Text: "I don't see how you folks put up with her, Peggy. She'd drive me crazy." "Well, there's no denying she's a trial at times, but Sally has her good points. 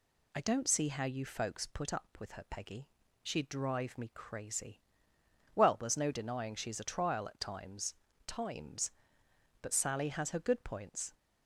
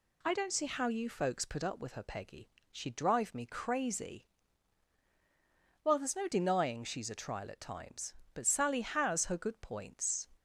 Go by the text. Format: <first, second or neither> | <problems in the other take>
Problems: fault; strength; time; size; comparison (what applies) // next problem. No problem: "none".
second | says "times" twice; at 8.2 s